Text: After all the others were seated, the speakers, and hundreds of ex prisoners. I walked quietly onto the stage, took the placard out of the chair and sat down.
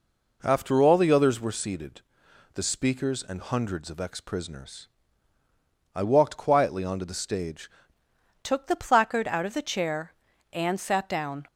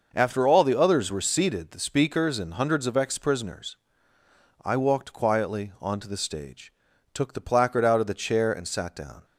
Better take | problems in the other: second | changes voice at "took"; from 8.4 s on; 3.0 s long

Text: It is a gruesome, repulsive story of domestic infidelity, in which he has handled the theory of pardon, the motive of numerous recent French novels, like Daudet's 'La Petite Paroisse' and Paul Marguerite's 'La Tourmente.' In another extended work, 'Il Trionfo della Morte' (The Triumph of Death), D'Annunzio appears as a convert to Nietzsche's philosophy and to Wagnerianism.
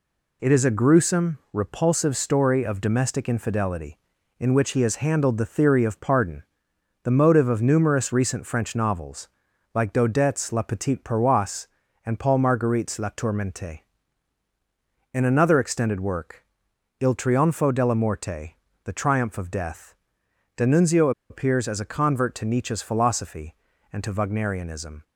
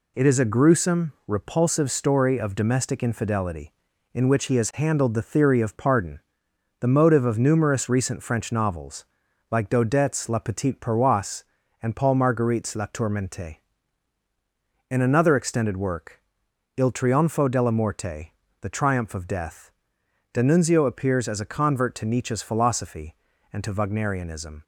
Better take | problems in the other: second | pauses between "D'Annunzio" and "appears"; slight; at 21.1 s; 0.19 s long

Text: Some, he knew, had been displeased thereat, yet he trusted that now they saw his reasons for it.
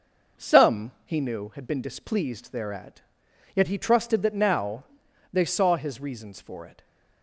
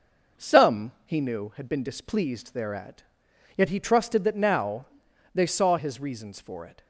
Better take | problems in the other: neither | pauses between "now" and "they"; noticeable; the same in both

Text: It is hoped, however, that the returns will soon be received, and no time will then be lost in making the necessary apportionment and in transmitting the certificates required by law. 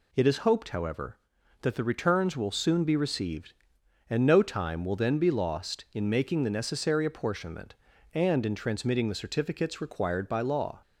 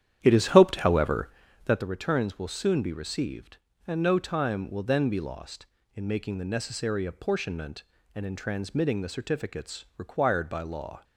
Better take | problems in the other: first | starts louder than the rest; strong; until 1.9 s; 10 dB

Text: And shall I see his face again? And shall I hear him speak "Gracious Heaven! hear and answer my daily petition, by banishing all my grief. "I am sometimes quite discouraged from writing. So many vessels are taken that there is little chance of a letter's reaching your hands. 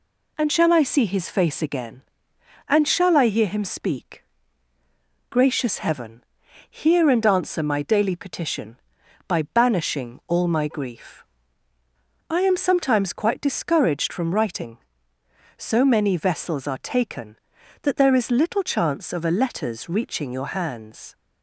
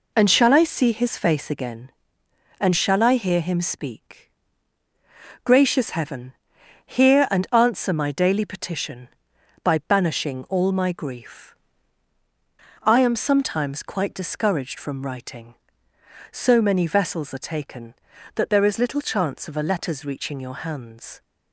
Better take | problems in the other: neither | pauses between "speak" and "Gracious"; the same in both

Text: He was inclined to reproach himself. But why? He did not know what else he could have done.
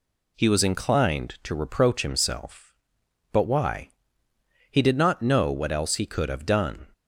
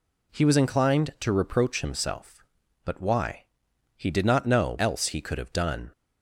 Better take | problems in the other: first | skips "what"; at 4.7 s

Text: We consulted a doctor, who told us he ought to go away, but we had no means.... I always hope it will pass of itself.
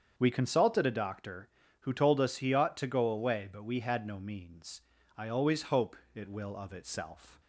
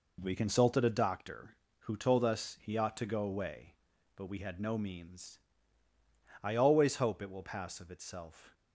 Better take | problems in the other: second | starts louder than the rest; strong; until 1.1 s; 7 dB // pauses between "hope" and "it"; slight; at 5.9 s; 0.18 s long // skips "pass"; at 6.5 s

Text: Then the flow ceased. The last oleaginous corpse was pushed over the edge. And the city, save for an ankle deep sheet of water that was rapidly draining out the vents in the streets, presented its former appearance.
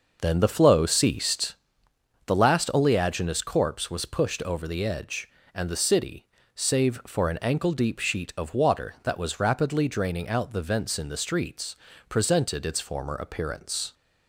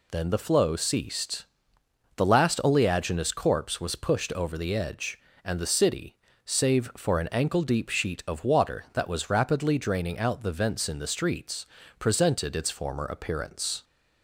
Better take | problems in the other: second | starts louder than the rest; noticeable; until 1.6 s; 5.5 dB

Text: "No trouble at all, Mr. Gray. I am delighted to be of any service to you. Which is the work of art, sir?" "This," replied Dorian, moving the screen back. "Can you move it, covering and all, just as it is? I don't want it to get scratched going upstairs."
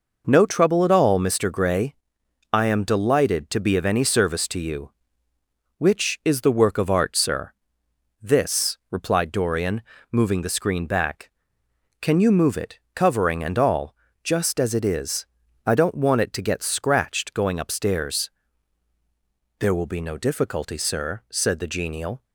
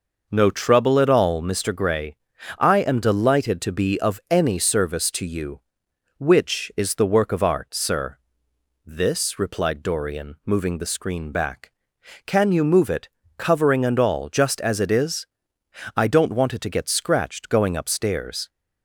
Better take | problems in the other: second | goes on to say "There will be no difficulty sir said the genial"; strong; from 19.5 s on; 2.6 s long

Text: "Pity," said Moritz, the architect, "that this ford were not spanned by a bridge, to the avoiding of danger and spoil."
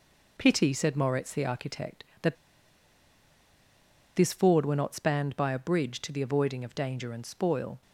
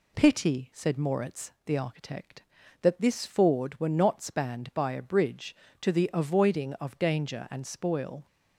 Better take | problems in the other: second | pauses between "that" and "this"; strong; at 2.3 s; 1.8 s long

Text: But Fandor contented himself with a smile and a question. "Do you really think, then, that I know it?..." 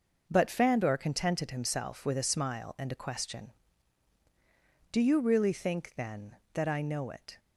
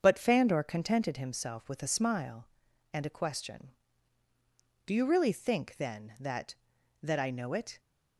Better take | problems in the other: first | starts louder than the rest; strong; until 1.0 s; 7 dB // says "that" twice; at 7.0 s

